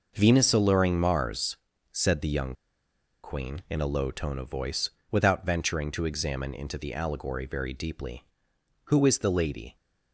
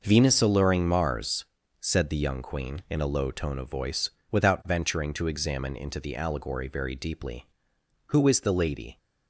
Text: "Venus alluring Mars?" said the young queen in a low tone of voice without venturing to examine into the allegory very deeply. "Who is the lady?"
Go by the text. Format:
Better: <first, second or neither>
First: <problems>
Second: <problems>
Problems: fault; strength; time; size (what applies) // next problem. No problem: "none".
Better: second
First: pauses between "young" and "queen"; noticeable; at 2.5 s; 0.70 s long // pauses between "voice" and "without"; slight; at 4.8 s; 0.22 s long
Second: pauses between "voice" and "without"; slight; at 4.0 s; 0.22 s long